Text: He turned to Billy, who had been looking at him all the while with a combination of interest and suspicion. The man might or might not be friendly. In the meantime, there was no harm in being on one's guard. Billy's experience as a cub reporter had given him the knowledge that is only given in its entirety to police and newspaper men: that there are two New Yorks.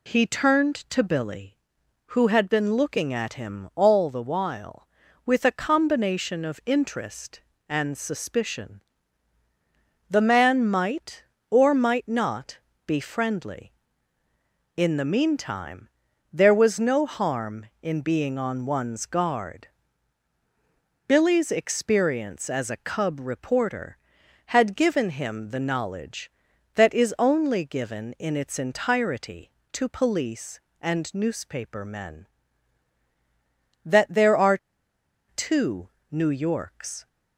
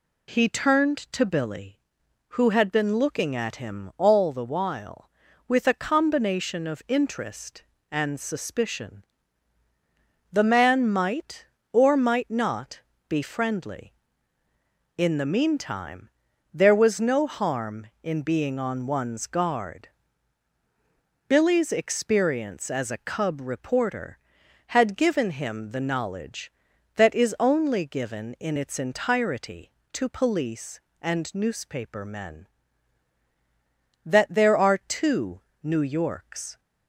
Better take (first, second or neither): second